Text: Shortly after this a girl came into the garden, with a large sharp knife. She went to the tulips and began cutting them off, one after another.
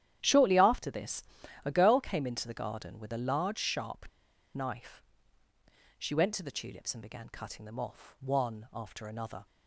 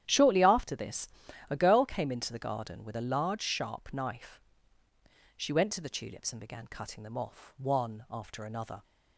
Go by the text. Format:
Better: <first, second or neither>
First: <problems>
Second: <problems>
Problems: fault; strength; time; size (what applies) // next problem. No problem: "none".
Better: second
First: starts louder than the rest; strong; until 1.2 s; 10.5 dB // pauses between "this" and "a"; at 1.2 s; 0.42 s long // pauses between "sharp" and "knife"; noticeable; at 4.0 s; 0.46 s long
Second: starts louder than the rest; strong; until 1.0 s; 10.5 dB // pauses between "this" and "a"; at 1.0 s; 0.42 s long